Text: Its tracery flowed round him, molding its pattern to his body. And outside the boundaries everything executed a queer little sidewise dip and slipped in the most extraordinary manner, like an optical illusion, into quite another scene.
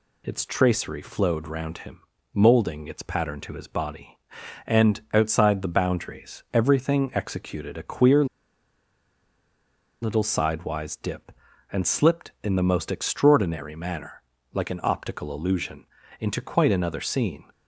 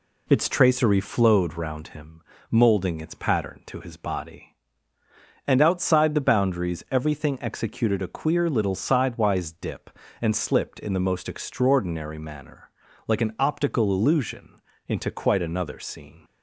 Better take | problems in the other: second | pauses between "queer" and "little"; strong; at 8.2 s; 1.7 s long

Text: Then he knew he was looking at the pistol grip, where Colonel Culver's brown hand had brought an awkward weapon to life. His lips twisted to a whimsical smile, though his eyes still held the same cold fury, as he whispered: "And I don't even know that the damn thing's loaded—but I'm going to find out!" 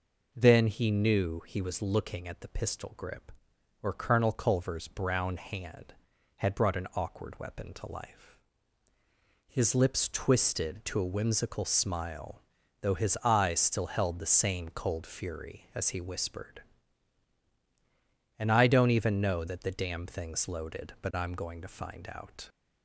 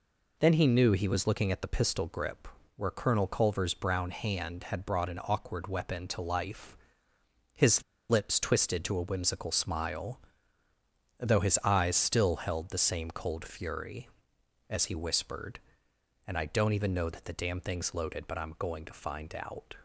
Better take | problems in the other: first | pauses between "His" and "lips"; slight; at 7.8 s; 0.26 s long

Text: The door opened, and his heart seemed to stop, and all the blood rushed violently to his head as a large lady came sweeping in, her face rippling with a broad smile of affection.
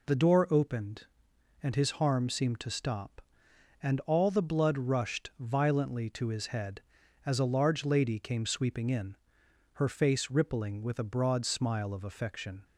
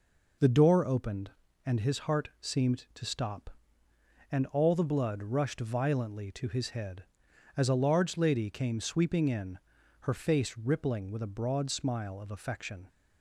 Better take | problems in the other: second | says "harm" for "heart"; at 1.9 s

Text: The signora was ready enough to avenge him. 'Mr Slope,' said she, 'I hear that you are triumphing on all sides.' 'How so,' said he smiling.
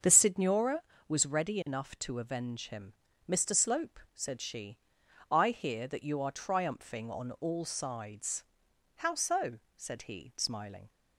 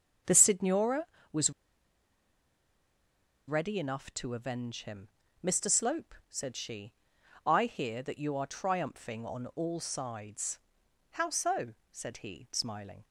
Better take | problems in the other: first | starts louder than the rest; strong; until 1.5 s; 7.5 dB; strong in the first // pauses between "was" and "ready"; strong; at 1.5 s; 1.9 s long

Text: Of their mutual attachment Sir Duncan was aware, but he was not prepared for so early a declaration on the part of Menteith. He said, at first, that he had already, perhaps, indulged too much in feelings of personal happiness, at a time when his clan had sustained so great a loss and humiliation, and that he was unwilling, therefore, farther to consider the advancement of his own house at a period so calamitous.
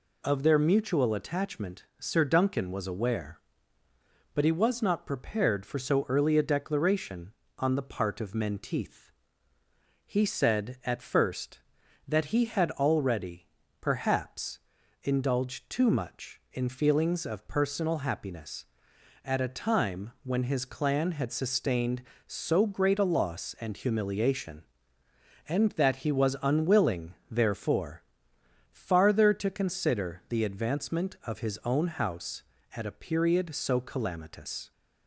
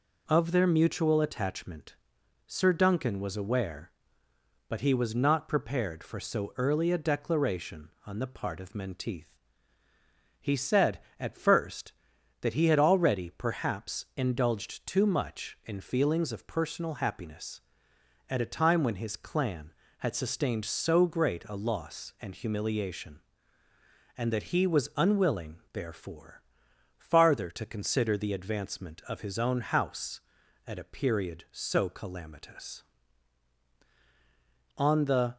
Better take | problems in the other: first | pauses between "attachment" and "Sir"; noticeable; at 1.9 s; 0.50 s long // goes on to say "On the"; from 34.7 s on; 0.58 s long

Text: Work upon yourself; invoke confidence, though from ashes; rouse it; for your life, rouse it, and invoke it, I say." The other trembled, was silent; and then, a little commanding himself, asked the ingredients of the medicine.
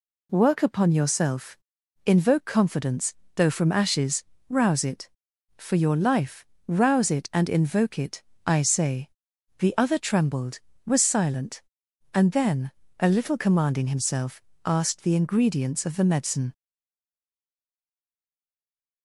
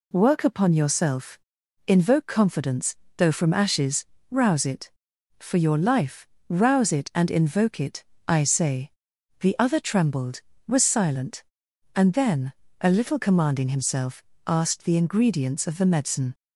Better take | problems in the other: second | stays silent after the last word; from 16.5 s on; 2.5 s long

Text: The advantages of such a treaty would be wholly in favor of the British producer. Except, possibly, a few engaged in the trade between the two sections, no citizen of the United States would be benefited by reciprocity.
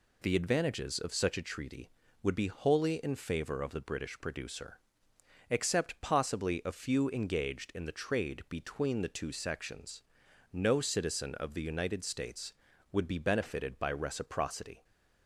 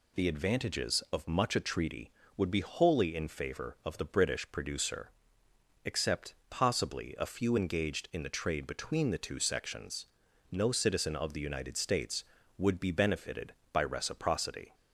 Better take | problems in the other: first | says "much" for "such"; at 1.2 s

